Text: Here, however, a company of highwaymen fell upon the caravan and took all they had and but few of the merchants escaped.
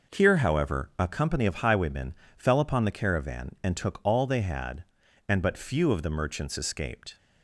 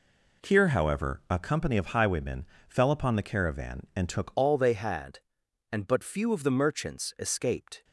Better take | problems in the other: first | pauses between "highwaymen" and "fell"; slight; at 2.4 s; 0.22 s long; slight in the first // changes voice at "all"; from 4.3 s on; 3.5 s long

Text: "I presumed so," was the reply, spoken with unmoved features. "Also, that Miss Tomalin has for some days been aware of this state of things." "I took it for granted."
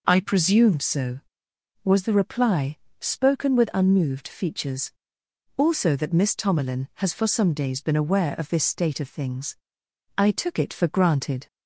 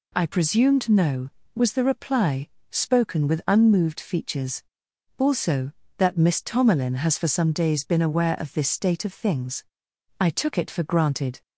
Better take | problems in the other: first | says "no" for "so"; at 0.8 s

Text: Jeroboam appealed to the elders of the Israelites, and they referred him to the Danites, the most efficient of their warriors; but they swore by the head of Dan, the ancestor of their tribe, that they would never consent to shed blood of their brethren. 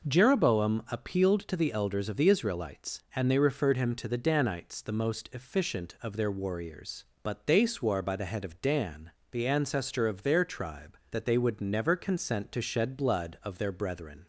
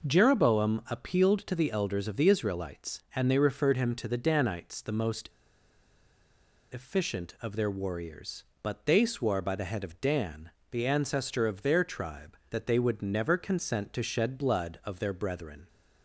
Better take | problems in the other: first | pauses between "most" and "efficient"; strong; at 5.2 s; 1.4 s long

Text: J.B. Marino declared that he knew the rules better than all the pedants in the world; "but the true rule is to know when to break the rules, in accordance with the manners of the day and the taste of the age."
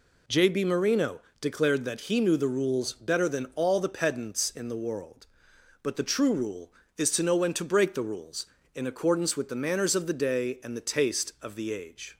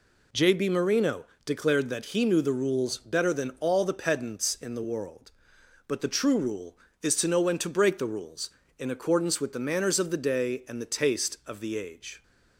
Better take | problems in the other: neither | pauses between "Marino" and "declared"; slight; the same in both

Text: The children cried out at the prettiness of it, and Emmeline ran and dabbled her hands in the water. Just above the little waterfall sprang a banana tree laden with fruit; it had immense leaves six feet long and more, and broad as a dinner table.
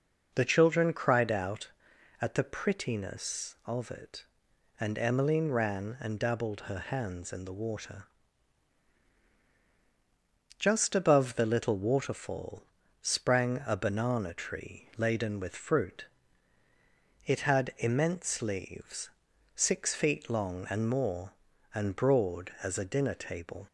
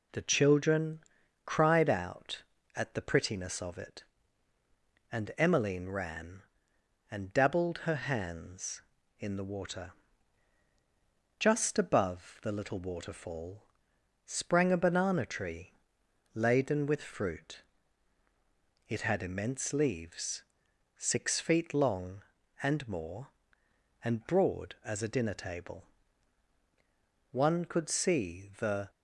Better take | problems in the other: first | pauses between "children" and "cried"; noticeable; at 0.9 s; 0.46 s long // pauses between "waterfall" and "sprang"; noticeable; at 13.6 s; 0.62 s long; also in the first // pauses between "tree" and "laden"; noticeable; at 15.7 s; 0.60 s long // pauses between "leaves" and "six"; noticeable; at 20.4 s; 0.56 s long; noticeable in the first // goes on to say "One could see the"; from 27.3 s on; 1.5 s long

